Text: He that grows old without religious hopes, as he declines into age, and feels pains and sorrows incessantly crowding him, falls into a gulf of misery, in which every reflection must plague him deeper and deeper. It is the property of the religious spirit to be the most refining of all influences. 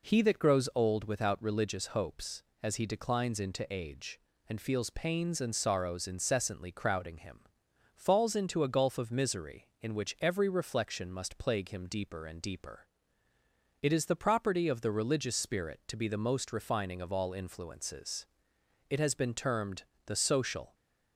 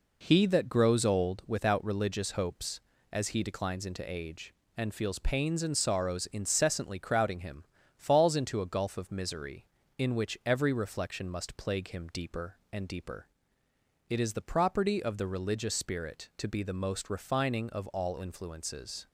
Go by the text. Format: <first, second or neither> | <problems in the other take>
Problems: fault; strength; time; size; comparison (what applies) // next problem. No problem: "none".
second | goes on to say "It has been termed the social"; strong; from 18.9 s on; 1.8 s long